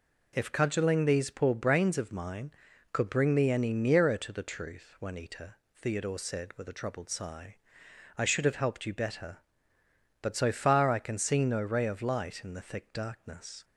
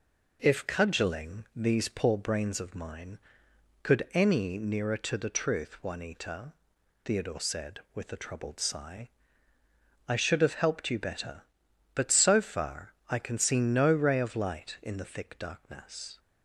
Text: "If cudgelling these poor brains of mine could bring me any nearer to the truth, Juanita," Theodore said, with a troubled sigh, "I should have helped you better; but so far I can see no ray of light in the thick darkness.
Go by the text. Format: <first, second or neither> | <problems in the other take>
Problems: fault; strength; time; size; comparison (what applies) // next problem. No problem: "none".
first | skips "bring me"; at 4.1 s